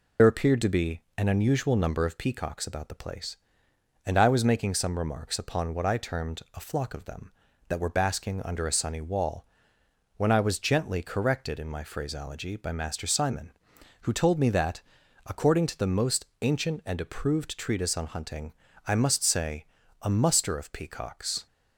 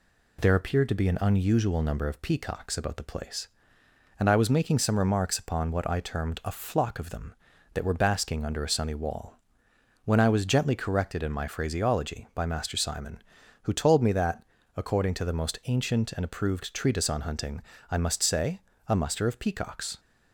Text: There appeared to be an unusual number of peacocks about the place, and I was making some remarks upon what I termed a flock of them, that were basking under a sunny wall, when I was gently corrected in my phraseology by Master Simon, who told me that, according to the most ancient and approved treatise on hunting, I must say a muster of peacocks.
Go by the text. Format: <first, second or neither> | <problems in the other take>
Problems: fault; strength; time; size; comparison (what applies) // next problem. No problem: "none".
second | loses the start of "There"; at 0.1 s; 60 ms // pauses between "most" and "ancient"; slight; at 16.2 s; 0.16 s long // pauses between "say" and "a"; slight; at 19.6 s; 0.36 s long; slight in the second